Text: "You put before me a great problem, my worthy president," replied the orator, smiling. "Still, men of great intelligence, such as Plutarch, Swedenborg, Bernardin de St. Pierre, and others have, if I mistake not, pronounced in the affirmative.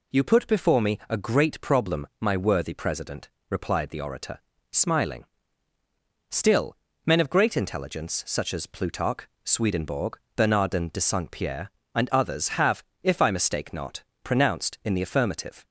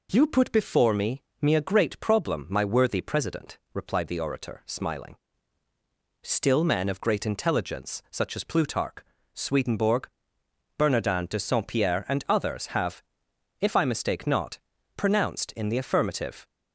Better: first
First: none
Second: says "me" twice; at 1.4 s

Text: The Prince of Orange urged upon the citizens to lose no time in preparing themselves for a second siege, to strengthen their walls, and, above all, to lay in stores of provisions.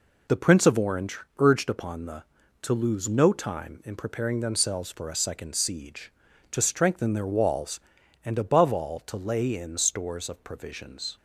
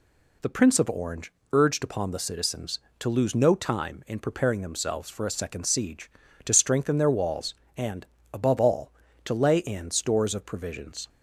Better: second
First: pauses between "Orange" and "urged"; slight; at 1.1 s; 0.18 s long // skips "citizens"; at 2.4 s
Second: pauses between "Orange" and "urged"; slight; at 1.3 s; 0.18 s long

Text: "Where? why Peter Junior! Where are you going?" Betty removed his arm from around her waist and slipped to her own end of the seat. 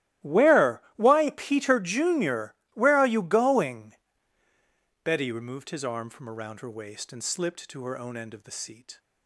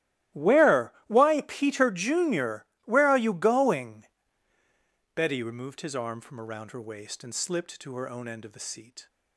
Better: neither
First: starts louder than the rest; strong; until 1.4 s; 15 dB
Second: starts louder than the rest; strong; until 1.5 s; 15 dB

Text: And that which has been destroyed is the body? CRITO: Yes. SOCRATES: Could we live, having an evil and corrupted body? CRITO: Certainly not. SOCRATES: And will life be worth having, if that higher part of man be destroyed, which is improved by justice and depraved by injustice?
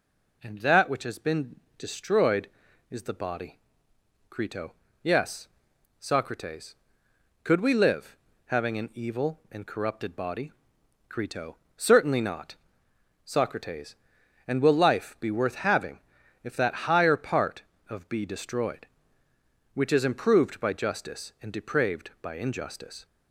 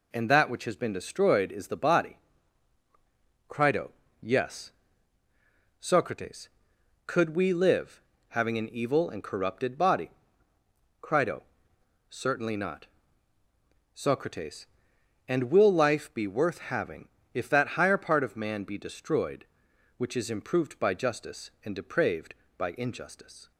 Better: second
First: pauses between "been" and "destroyed"; slight; at 1.5 s; 0.20 s long // skips "man"; at 18.0 s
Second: none

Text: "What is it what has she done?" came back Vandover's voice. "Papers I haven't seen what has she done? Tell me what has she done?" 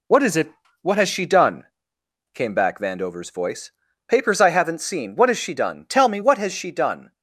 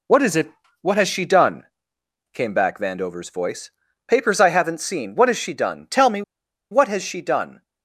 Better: first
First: pauses between "it" and "what"; slight; at 0.5 s; 0.30 s long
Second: pauses between "it" and "what"; slight; at 0.5 s; 0.30 s long // pauses between "me" and "what"; noticeable; at 6.2 s; 0.49 s long

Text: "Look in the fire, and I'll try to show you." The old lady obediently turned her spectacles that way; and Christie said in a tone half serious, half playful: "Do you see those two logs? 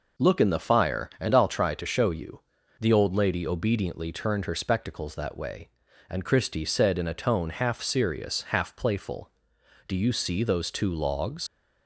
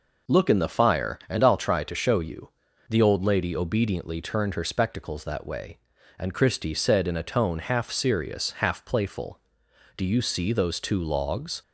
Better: second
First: leaves "logs" unfinished; at 11.4 s; 55 ms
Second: none

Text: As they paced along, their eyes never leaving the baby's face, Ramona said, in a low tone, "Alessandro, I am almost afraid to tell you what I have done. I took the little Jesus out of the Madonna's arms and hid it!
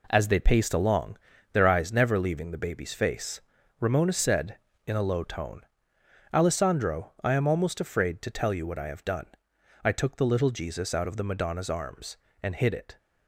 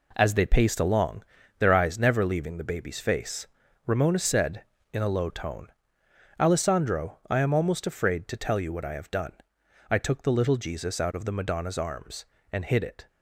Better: neither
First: none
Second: none

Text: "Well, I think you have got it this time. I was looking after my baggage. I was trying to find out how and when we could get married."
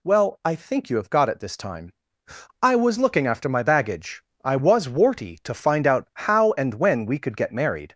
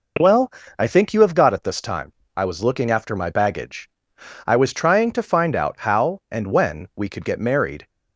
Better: second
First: says "warty" for "trying"; at 4.8 s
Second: none

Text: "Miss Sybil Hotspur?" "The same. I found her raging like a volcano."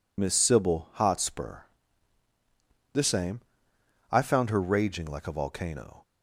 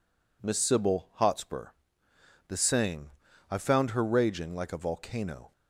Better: second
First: loses the start of "Miss"; at 0.1 s; 35 ms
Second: none

